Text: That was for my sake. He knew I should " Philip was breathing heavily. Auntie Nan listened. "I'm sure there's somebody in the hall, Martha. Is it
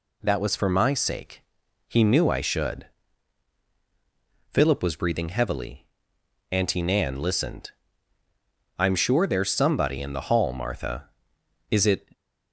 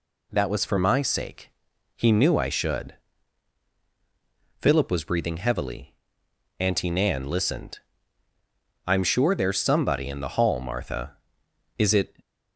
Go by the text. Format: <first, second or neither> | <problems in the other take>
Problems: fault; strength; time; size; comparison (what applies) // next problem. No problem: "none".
neither | none